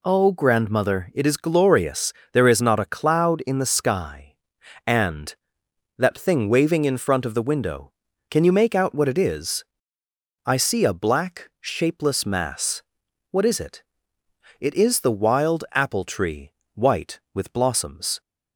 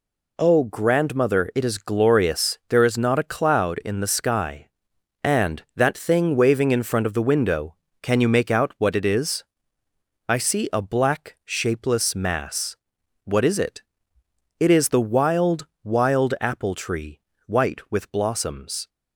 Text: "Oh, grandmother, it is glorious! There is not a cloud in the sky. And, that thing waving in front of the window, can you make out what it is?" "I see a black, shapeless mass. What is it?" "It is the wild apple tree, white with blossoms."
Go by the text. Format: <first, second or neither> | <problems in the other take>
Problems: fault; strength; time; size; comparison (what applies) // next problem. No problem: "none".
first | says "wild" twice; at 15.8 s